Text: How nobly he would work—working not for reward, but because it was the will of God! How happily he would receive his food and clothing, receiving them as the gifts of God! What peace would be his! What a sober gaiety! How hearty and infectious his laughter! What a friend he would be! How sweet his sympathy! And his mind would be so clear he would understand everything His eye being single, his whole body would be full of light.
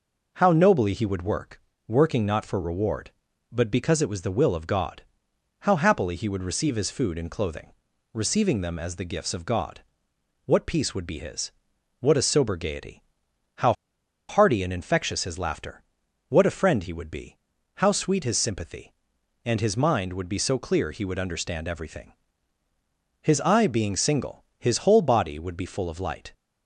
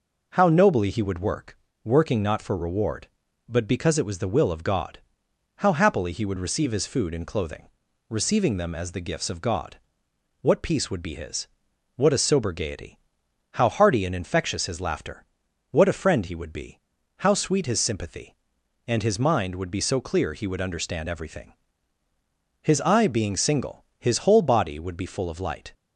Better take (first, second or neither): second